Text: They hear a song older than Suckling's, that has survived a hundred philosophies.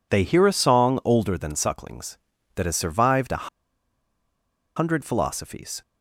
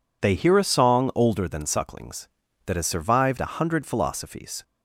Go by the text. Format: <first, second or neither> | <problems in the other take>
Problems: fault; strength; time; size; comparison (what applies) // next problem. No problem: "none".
second | pauses between "a" and "hundred"; strong; at 3.4 s; 1.2 s long